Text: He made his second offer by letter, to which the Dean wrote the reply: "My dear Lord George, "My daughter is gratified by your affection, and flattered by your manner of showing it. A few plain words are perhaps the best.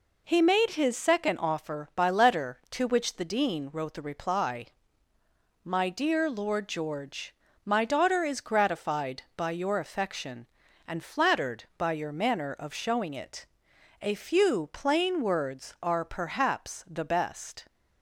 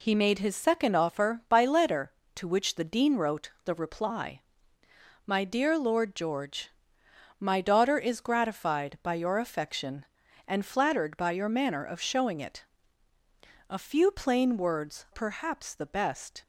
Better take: first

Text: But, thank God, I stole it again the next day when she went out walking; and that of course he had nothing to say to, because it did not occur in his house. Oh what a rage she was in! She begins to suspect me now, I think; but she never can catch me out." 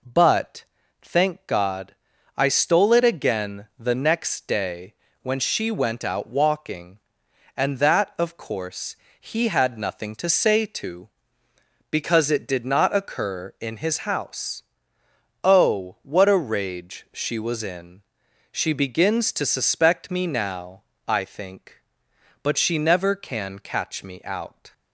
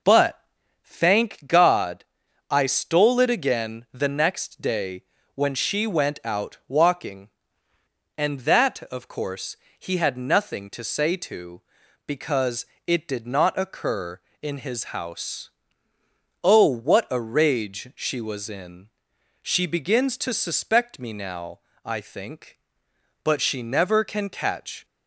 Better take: first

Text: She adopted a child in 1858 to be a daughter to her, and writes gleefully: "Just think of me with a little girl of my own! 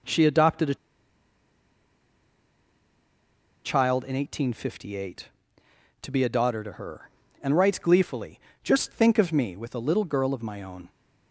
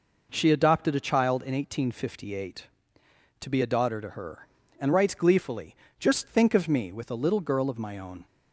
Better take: second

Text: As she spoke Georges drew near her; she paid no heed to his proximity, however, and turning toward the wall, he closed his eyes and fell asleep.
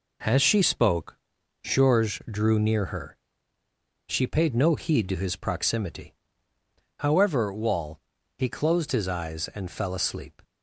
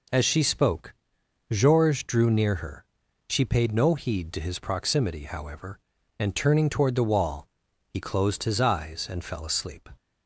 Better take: second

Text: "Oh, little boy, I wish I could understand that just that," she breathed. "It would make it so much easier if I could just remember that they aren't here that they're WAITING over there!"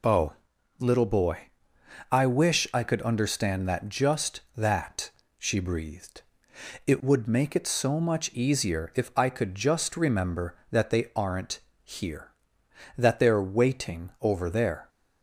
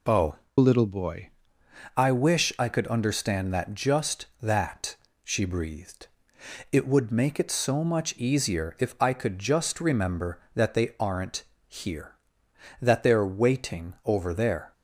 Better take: first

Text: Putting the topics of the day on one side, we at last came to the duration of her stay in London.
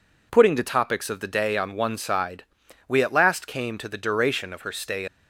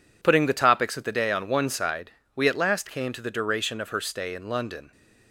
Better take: second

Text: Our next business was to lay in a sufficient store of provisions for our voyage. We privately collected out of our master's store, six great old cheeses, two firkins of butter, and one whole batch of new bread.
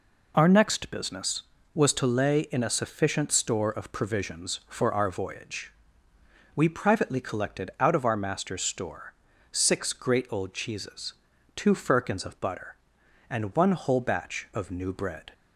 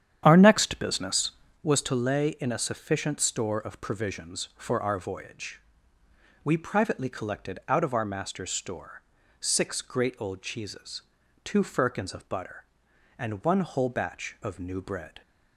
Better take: first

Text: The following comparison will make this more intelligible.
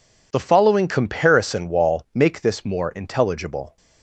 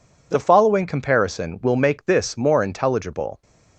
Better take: second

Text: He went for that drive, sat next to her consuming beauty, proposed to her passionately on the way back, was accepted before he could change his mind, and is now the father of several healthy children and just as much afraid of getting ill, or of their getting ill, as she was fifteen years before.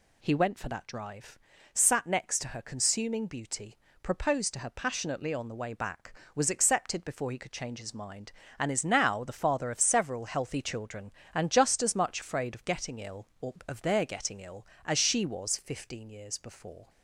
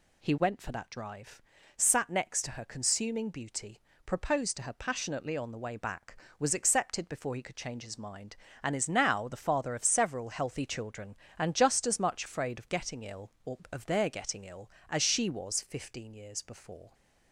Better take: neither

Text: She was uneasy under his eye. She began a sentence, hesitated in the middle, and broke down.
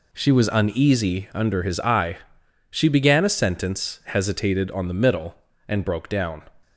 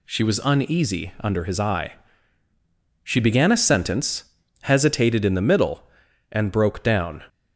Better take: second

